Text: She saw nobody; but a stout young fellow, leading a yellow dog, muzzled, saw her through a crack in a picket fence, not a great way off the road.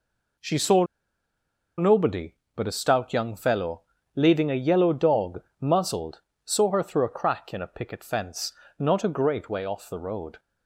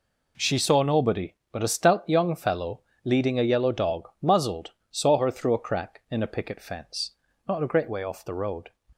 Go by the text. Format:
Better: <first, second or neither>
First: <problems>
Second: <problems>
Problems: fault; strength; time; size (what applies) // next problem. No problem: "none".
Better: second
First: pauses between "saw" and "nobody"; noticeable; at 0.8 s; 0.94 s long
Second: none